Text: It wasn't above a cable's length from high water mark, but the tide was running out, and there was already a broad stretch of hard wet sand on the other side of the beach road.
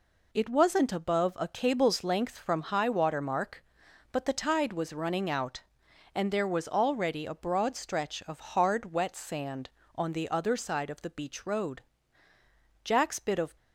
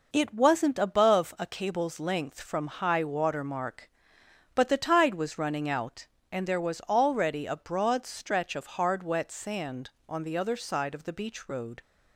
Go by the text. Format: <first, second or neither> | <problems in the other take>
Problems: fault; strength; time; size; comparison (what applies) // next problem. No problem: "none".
second | goes on to say "Jack's bit of"; noticeable; from 12.8 s on; 0.72 s long